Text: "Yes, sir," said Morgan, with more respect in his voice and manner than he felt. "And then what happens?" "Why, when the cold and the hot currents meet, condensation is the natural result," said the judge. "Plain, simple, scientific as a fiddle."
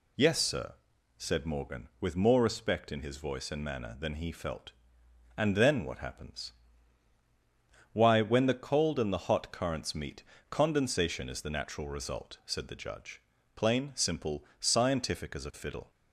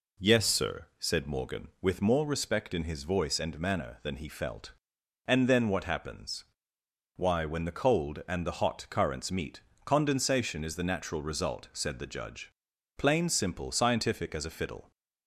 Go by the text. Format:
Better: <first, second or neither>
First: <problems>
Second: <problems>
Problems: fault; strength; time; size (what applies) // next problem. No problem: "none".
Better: neither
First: none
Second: none